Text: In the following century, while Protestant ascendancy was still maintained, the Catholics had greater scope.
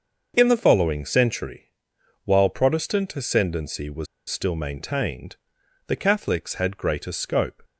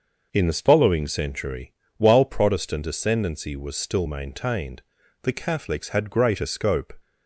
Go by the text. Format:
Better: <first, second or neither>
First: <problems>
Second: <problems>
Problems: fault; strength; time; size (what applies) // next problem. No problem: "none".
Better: second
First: starts louder than the rest; until 1.3 s; 6.5 dB // pauses between "was" and "still"; slight; at 4.0 s; 0.23 s long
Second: none